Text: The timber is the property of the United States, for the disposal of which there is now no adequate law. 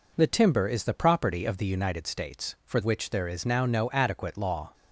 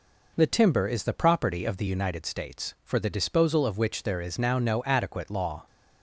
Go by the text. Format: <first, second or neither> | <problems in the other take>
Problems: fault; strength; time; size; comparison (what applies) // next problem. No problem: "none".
second | skips "the disposal of"; at 2.8 s